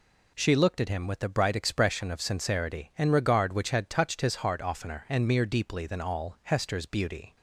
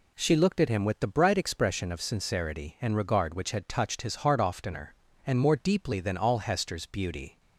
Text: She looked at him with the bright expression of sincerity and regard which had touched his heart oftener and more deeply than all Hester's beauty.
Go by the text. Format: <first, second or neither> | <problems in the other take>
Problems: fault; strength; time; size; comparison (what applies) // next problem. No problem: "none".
second | says "mere" for "more"; at 5.2 s